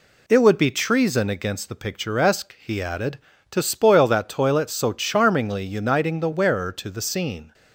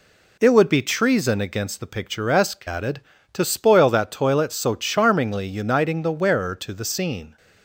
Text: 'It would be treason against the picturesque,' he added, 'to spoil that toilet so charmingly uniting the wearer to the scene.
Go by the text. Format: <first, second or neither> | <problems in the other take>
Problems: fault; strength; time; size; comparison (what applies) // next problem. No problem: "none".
first | skips "he"; at 2.6 s